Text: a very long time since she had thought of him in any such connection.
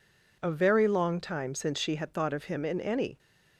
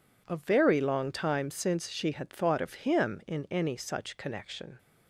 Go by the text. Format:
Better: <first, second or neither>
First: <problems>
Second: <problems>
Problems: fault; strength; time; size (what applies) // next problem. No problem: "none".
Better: second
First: stops before "such connection"; at 3.1 s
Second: none